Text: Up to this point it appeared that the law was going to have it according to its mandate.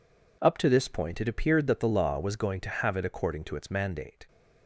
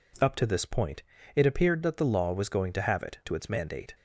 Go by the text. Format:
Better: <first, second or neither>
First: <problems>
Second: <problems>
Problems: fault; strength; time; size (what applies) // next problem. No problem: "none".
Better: first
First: none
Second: pauses between "point" and "it"; slight; at 1.0 s; 0.32 s long // skips "according"; at 3.2 s